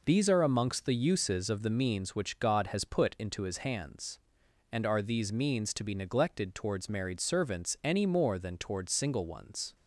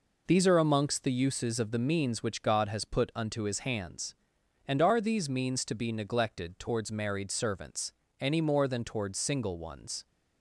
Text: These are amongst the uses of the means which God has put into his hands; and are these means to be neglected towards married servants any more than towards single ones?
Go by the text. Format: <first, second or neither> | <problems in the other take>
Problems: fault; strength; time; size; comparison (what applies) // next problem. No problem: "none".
first | says "unto" for "into"; at 3.1 s // pauses between "servants" and "any"; slight; at 7.9 s; 0.28 s long